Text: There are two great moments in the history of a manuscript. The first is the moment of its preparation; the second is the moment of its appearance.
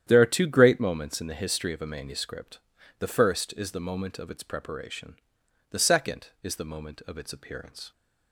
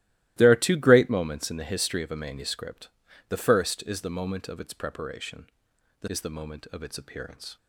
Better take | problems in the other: first | starts louder than the rest; strong; until 1.3 s; 16 dB; strong in the first // skips "second"; at 6.0 s

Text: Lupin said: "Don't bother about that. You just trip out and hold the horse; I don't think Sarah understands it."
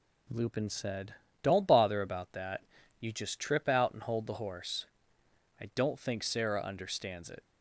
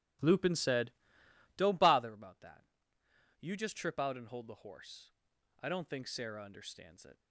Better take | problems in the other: first | starts louder than the rest; strong; until 1.7 s; 12.5 dB

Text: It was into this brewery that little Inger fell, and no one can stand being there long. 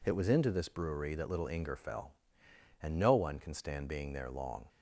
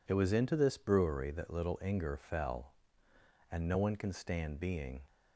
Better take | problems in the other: first | stops before "there long"; at 5.0 s

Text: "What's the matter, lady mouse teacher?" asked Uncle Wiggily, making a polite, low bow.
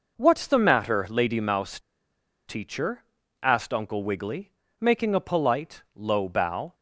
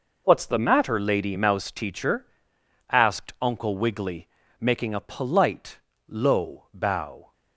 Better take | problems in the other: second | pauses between "mouse" and "teacher"; noticeable; at 1.7 s; 0.68 s long

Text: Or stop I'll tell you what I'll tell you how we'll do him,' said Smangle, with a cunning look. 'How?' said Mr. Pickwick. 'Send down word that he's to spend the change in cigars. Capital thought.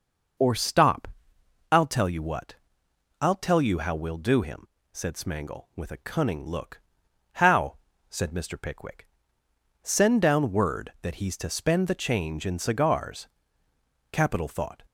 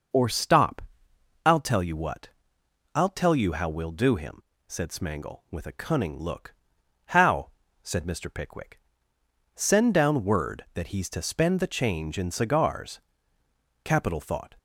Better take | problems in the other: neither | pauses between "stop" and "I'll"; noticeable; the same in both // pauses between "what" and "I'll"; noticeable; the same in both

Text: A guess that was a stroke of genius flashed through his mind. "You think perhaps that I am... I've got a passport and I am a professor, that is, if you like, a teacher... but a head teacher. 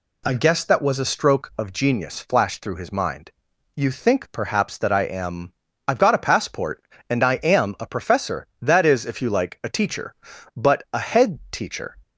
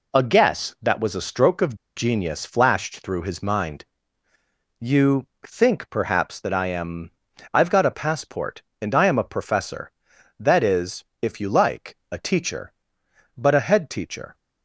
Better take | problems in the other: first | pauses between "of" and "genius"; slight; at 1.7 s; 0.20 s long // pauses between "You" and "think"; slight; at 5.2 s; 0.18 s long

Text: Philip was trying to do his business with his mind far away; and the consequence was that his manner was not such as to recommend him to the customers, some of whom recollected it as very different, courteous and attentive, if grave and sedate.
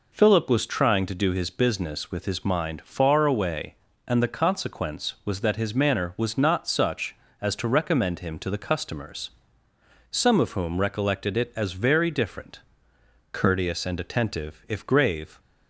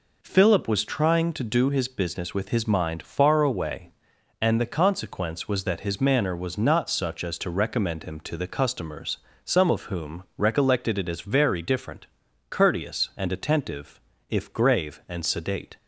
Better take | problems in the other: second | stops before "and sedate"; at 15.3 s

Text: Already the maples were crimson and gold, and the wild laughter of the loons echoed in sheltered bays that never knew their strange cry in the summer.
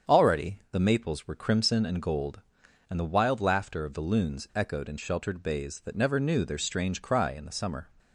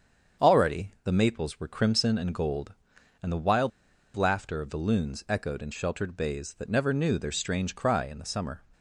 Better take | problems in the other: first | starts louder than the rest; strong; until 1.5 s; 7.5 dB; strong in the first // pauses between "wild" and "laughter"; at 3.7 s; 0.45 s long

